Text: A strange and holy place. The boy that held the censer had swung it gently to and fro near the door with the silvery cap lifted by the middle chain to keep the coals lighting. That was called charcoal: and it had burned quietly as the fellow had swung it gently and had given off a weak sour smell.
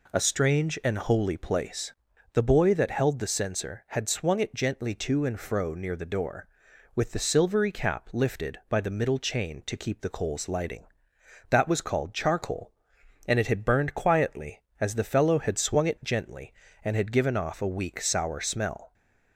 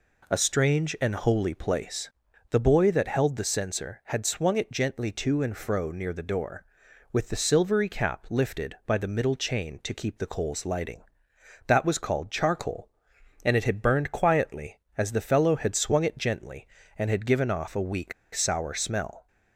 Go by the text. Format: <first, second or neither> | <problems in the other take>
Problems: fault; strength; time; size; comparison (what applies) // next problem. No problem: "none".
first | pauses between "weak" and "sour"; slight; at 18.1 s; 0.22 s long